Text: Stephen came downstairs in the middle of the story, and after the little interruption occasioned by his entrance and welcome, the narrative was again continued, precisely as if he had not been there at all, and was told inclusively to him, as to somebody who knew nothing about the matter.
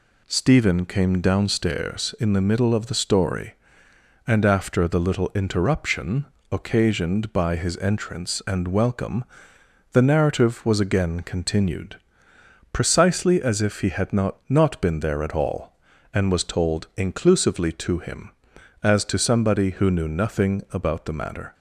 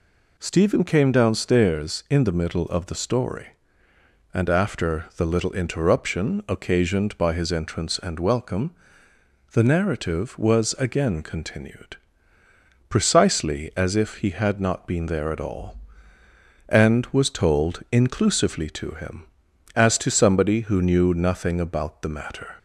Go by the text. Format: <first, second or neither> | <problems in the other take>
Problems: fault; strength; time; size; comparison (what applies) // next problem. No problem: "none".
second | pauses between "interruption" and "occasioned"; slight; at 6.2 s; 0.26 s long // says "not" twice; at 14.4 s